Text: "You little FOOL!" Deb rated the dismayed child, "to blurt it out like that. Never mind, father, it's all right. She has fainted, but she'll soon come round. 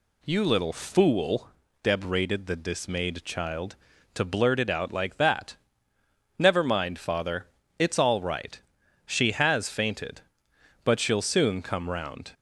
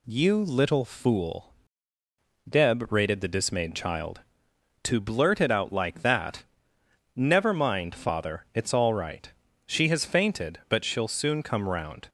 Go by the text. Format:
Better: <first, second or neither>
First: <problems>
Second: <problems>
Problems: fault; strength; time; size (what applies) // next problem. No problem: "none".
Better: neither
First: none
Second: none